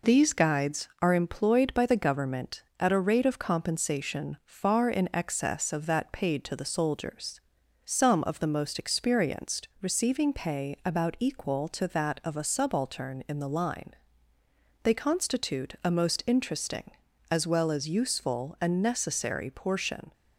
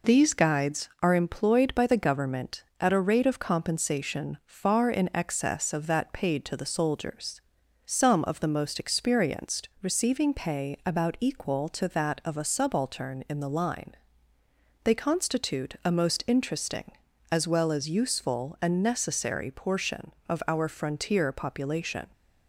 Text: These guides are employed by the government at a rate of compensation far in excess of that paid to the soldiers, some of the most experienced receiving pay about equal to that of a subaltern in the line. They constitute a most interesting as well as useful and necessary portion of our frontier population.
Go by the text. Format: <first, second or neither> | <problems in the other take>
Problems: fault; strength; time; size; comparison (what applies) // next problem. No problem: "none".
second | stops before "of our frontier population"; at 20.1 s